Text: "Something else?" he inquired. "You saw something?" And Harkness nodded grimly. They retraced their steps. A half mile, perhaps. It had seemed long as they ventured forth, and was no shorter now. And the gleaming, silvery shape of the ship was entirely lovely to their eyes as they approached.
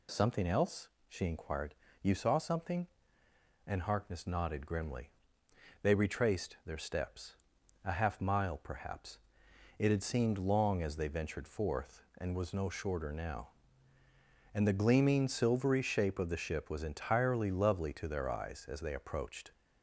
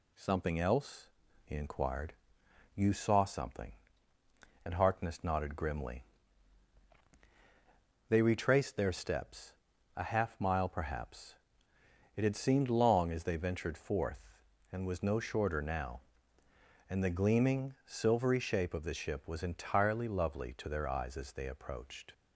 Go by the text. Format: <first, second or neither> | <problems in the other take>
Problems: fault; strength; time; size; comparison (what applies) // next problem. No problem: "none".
second | says "she" for "he"; at 1.0 s